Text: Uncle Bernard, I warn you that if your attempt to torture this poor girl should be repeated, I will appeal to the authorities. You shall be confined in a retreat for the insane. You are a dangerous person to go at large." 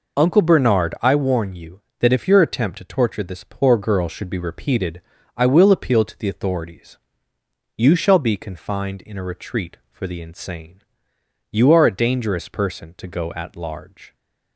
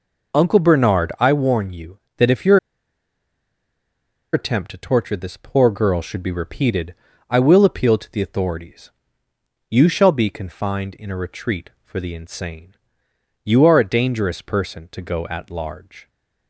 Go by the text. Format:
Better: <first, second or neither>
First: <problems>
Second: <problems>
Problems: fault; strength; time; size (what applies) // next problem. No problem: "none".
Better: first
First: none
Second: pauses between "your" and "attempt"; strong; at 2.5 s; 1.7 s long